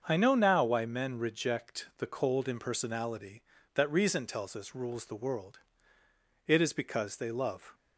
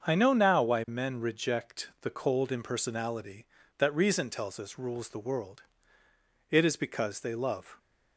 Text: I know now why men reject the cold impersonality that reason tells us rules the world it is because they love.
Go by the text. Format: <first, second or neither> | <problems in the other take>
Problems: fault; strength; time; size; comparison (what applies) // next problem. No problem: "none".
neither | starts louder than the rest; the same in both // pauses between "world" and "it"; noticeable; the same in both